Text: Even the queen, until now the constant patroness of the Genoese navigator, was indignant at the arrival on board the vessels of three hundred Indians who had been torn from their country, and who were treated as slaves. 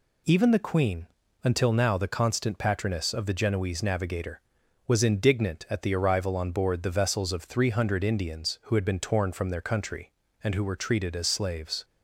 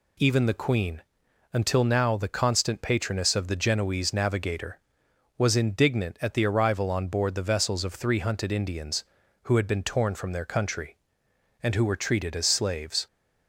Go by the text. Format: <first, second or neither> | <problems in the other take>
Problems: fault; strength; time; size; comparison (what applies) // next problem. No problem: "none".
first | says "hunted" for "hundred"; at 8.1 s